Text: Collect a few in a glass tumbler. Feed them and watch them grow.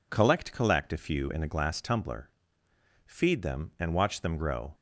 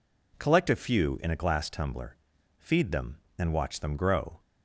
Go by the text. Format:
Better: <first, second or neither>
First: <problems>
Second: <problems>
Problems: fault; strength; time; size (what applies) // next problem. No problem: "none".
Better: second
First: says "Collect" twice; at 0.5 s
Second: none